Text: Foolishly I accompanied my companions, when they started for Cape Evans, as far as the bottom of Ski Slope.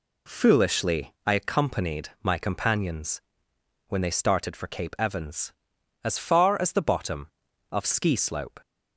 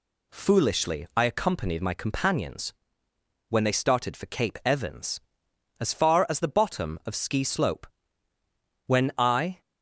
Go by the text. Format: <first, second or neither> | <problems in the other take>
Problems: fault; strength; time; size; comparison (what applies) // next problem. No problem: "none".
first | goes on to say "When I"; noticeable; from 8.8 s on; 0.74 s long